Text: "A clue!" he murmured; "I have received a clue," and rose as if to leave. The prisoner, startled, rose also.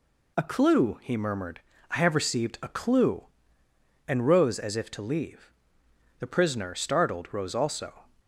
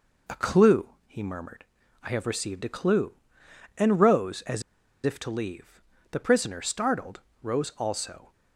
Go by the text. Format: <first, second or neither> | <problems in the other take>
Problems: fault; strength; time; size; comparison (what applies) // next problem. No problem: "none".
first | pauses between "as" and "if"; at 4.6 s; 0.43 s long